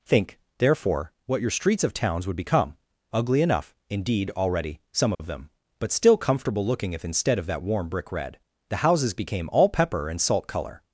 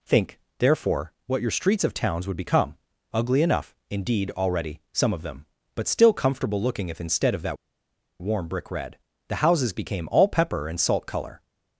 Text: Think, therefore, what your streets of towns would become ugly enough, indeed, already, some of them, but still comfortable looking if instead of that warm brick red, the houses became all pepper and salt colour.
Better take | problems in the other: first | pauses between "become" and "ugly"; at 2.7 s; 0.38 s long; also in the first // pauses between "that" and "warm"; noticeable; at 7.5 s; 0.65 s long

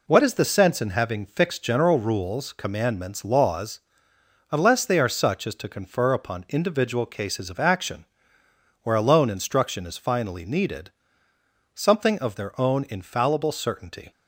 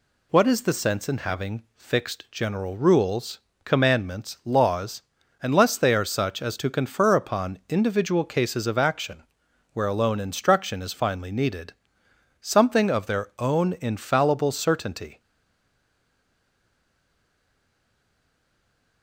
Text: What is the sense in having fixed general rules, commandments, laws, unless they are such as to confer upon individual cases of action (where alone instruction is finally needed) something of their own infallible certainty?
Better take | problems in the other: first | stays silent after the last word; strong; from 15.1 s on; 3.9 s long

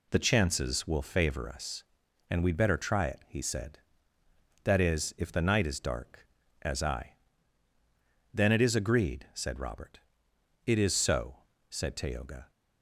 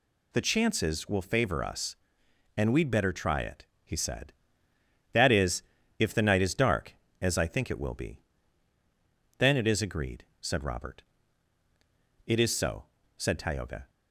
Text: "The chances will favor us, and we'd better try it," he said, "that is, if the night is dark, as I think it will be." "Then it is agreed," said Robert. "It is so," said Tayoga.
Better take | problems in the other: second | skips "think it will be"; at 7.7 s

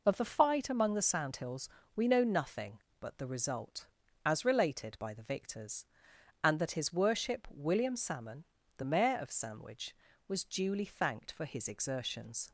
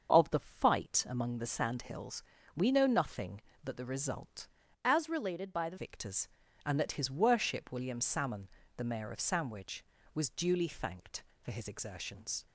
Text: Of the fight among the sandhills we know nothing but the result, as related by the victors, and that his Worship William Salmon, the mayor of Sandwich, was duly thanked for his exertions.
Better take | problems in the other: first | starts louder than the rest; until 1.1 s; 6.5 dB // pauses between "sandhills" and "we"; slight; at 2.2 s; 0.36 s long; slight in the first // changes voice from "as" to "the"; from 4.8 to 5.7 s; 0.9 s long

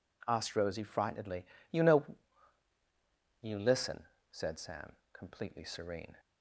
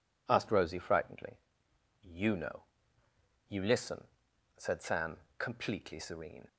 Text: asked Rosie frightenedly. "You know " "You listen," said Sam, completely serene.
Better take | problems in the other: neither | none

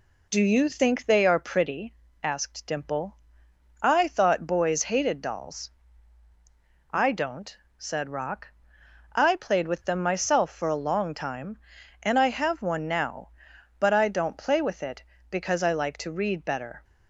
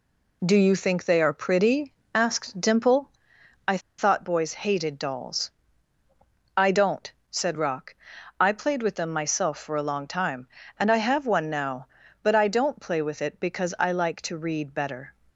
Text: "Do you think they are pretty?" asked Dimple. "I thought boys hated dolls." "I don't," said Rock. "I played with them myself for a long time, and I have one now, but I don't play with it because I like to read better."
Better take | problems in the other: first | pauses between "I" and "thought"; slight; at 3.7 s; 0.19 s long

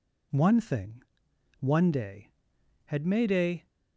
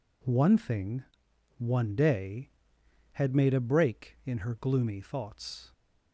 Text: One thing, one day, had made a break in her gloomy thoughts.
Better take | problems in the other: second | stops before "break in her gloomy thoughts"; at 3.6 s

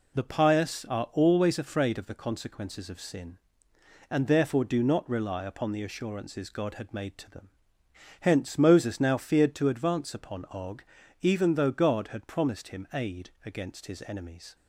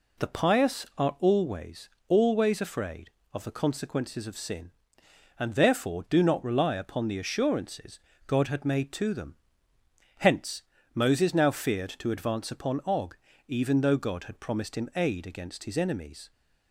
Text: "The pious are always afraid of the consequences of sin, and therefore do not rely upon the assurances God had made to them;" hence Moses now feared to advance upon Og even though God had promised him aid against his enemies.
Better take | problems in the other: first | says "always" twice; at 2.0 s // pauses between "assurances" and "God"; slight; at 7.9 s; 0.26 s long // pauses between "hence" and "Moses"; slight; at 10.6 s; 0.28 s long // pauses between "Og" and "even"; slight; at 13.1 s; 0.30 s long; also in the first

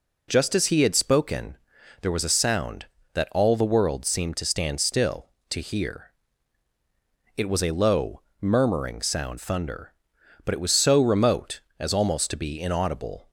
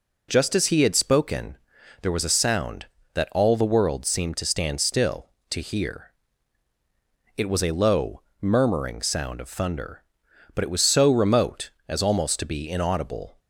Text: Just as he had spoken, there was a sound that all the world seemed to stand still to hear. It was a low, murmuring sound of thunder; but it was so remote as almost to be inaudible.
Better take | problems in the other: second | skips "of"; at 9.3 s

